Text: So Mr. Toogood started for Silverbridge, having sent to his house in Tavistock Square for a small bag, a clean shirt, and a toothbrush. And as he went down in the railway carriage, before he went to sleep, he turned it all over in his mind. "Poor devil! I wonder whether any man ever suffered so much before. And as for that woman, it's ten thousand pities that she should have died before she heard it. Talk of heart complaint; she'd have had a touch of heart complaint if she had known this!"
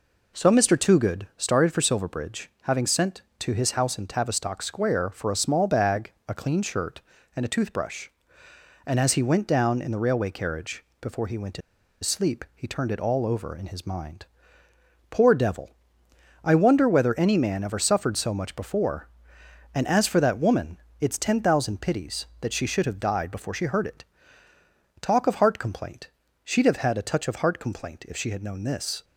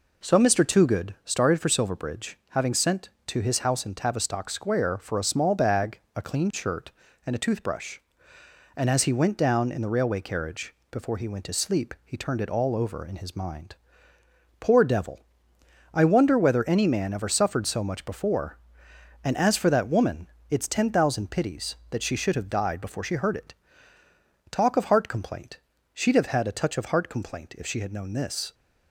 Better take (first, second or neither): second